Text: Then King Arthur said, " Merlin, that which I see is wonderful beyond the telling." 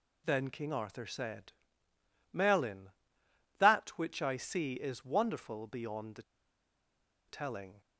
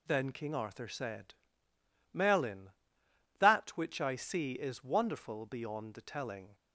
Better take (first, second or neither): second